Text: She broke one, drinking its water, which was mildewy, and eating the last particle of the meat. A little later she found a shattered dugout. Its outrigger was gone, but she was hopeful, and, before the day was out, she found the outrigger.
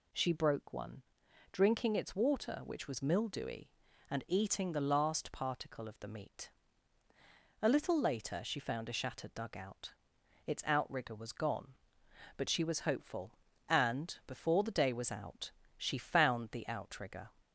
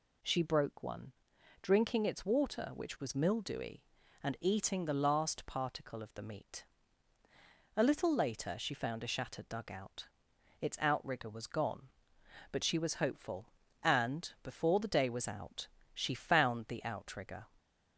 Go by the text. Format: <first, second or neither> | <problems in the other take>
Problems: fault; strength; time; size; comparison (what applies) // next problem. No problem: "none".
neither | none